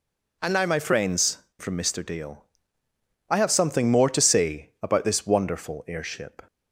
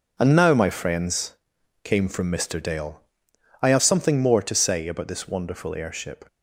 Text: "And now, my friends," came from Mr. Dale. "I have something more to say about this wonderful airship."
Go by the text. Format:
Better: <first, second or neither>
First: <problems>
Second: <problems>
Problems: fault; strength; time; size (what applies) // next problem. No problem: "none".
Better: second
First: skips "came"; at 1.4 s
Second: none